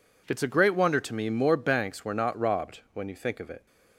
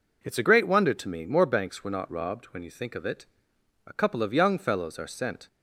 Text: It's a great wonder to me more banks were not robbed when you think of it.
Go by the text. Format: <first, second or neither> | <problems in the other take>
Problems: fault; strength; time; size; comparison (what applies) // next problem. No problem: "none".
first | goes on to say "A couple of young fellows are sent"; from 3.8 s on; 1.6 s long